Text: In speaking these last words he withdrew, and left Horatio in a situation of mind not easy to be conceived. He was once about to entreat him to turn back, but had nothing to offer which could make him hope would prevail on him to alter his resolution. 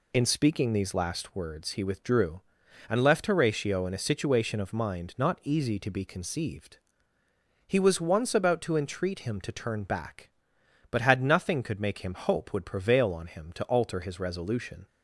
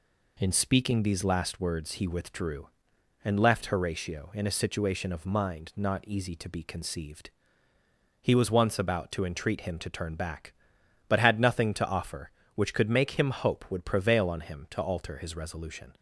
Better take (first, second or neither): second